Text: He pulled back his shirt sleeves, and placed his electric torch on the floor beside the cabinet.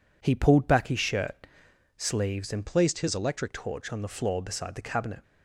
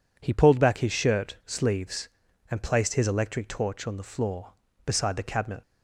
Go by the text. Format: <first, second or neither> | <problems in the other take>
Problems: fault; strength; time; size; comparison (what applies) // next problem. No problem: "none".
second | pauses between "shirt" and "sleeves"; noticeable; at 1.3 s; 0.62 s long // changes voice from "placed" to "electric"; from 2.6 to 3.5 s; 0.9 s long